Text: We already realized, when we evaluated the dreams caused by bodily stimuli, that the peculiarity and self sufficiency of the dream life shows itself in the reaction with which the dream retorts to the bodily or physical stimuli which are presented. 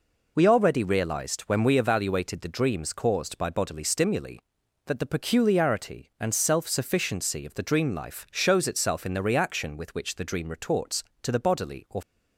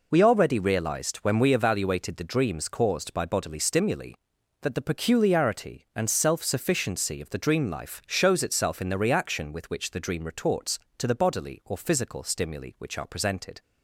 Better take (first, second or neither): second